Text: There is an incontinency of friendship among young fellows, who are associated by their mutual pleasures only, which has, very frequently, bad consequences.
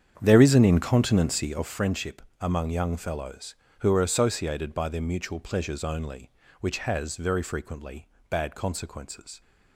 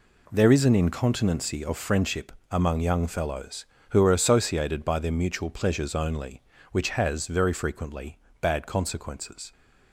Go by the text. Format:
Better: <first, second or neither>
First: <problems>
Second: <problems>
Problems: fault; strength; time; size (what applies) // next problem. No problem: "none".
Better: second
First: starts louder than the rest; strong; until 1.7 s; 8 dB // pauses between "friendship" and "among"; slight; at 2.2 s; 0.18 s long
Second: pauses between "friendship" and "among"; slight; at 2.3 s; 0.18 s long